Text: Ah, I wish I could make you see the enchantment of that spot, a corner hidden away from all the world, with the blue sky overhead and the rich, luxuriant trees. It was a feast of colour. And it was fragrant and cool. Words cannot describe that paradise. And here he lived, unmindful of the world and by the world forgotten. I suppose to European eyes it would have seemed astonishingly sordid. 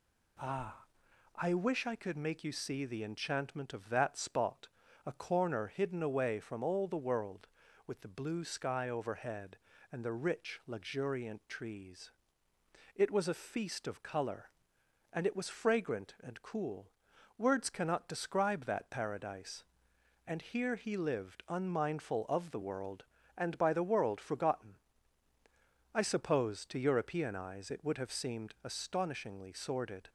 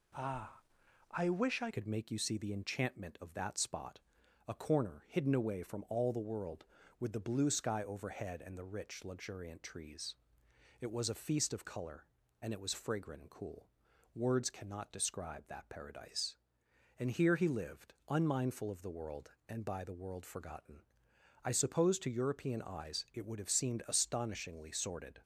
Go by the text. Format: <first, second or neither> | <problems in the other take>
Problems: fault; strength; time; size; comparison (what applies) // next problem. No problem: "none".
first | changes voice at "could"; from 1.7 s on; 23.5 s long